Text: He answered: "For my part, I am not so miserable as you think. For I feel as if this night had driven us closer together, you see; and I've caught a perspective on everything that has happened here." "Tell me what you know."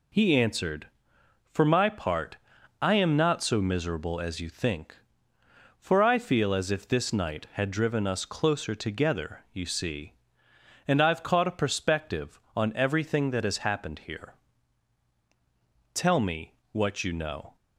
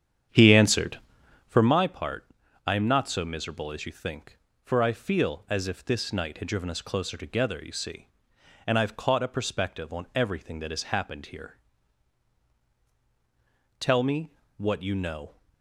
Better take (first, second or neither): first